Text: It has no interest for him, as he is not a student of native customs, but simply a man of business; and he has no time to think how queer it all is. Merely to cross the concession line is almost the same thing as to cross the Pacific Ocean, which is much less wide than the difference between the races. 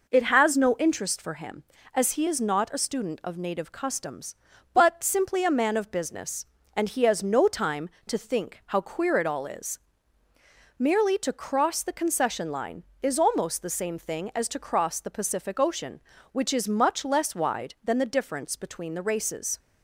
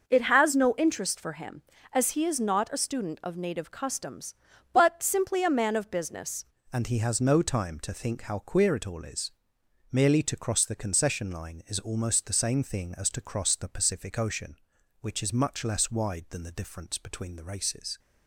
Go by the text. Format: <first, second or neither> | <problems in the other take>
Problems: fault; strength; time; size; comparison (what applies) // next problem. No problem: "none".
first | starts louder than the rest; noticeable; until 1.1 s; 6 dB // changes voice at "and"; from 6.7 s on; 11.2 s long